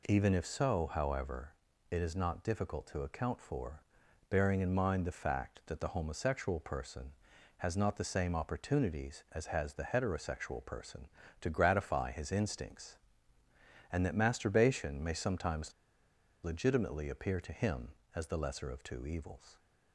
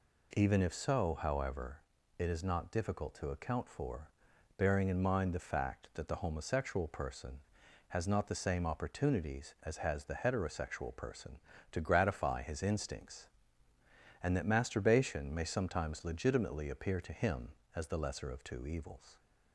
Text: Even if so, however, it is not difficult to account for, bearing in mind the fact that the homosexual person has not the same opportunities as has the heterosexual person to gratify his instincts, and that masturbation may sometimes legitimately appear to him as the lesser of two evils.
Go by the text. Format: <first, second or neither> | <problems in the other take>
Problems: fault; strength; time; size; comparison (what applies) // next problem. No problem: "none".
second | pauses between "sometimes" and "legitimately"; noticeable; at 15.7 s; 0.71 s long